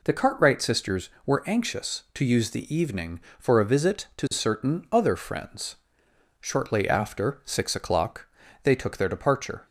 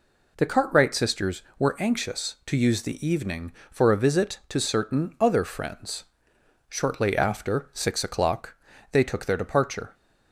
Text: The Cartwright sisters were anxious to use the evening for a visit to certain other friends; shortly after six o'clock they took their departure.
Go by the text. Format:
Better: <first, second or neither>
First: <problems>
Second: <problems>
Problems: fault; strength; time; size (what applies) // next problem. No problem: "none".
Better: neither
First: pauses between "o'clock" and "they"; slight; at 8.2 s; 0.34 s long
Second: pauses between "o'clock" and "they"; slight; at 8.5 s; 0.34 s long